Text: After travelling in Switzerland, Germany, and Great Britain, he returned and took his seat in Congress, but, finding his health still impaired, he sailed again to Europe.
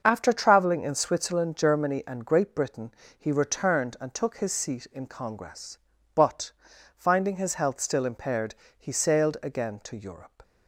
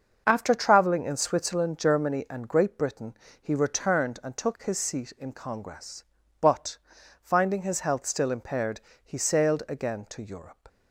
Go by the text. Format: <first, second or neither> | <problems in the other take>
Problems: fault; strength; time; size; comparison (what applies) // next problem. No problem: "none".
neither | starts louder than the rest; the same in both